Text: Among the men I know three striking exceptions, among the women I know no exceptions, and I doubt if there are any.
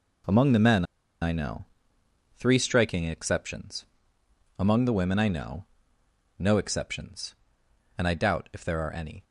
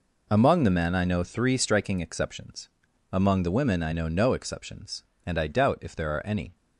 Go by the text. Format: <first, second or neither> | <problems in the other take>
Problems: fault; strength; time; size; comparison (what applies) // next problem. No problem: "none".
second | pauses between "men" and "I"; at 0.8 s; 0.38 s long // pauses between "know" and "three"; noticeable; at 1.6 s; 0.72 s long // pauses between "know" and "no"; noticeable; at 5.6 s; 0.72 s long